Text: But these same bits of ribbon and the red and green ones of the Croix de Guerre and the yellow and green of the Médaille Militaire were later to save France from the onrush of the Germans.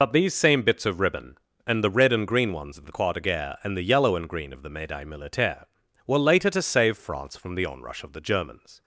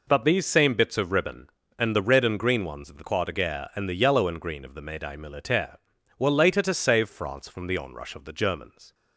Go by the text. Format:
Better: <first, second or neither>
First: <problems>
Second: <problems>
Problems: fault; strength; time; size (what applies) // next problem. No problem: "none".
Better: second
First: loses the start of "But"; at 0.0 s; 45 ms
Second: none